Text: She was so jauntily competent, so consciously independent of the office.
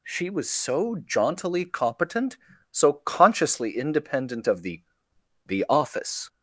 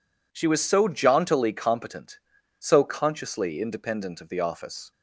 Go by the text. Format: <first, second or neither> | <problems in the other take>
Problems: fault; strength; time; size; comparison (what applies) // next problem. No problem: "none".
second | says "the" twice; at 5.4 s